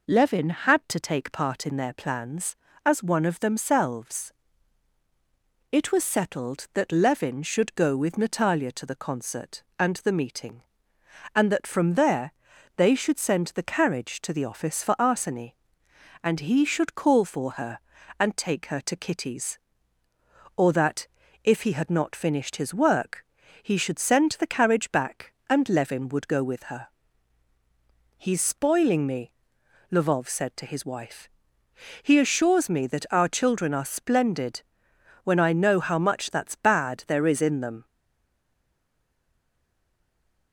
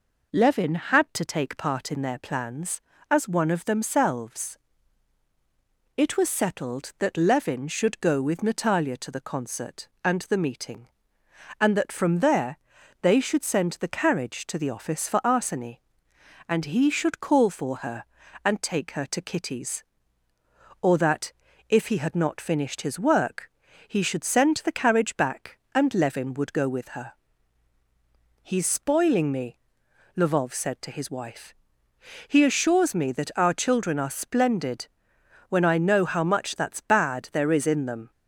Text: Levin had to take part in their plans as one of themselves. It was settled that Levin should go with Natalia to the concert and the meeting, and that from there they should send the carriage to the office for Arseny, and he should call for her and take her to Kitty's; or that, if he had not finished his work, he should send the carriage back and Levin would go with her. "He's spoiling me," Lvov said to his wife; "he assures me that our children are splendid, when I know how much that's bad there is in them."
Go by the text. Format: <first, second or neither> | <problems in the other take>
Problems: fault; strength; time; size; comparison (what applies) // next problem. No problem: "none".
second | pauses between "there" and "they"; at 12.3 s; 0.42 s long; also in the second // stays silent after the last word; strong; from 37.8 s on; 2.7 s long